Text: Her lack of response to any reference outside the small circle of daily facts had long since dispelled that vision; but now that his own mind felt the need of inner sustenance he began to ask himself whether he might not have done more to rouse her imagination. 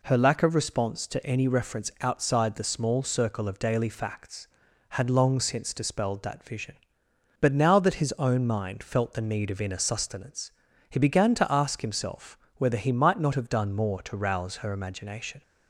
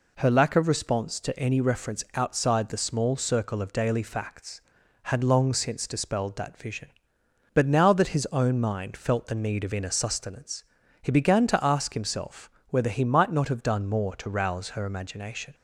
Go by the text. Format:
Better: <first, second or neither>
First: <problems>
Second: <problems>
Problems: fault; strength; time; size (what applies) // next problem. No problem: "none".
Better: neither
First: pauses between "sustenance" and "he"; at 10.5 s; 0.38 s long // pauses between "himself" and "whether"; slight; at 12.3 s; 0.20 s long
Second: pauses between "sustenance" and "he"; at 10.6 s; 0.38 s long // pauses between "himself" and "whether"; slight; at 12.4 s; 0.20 s long